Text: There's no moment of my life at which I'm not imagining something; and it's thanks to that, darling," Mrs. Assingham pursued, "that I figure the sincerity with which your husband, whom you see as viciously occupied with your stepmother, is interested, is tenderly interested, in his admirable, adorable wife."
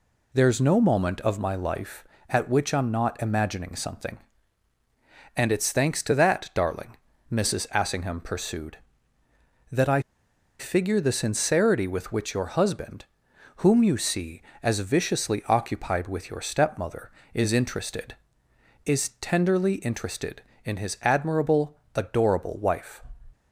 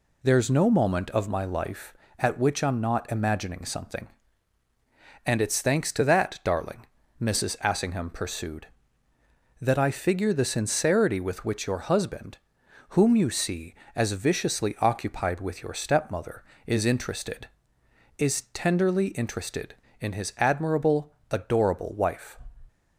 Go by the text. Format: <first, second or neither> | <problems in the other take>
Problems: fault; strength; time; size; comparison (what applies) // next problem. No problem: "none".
second | pauses between "I" and "figure"; noticeable; at 10.0 s; 0.57 s long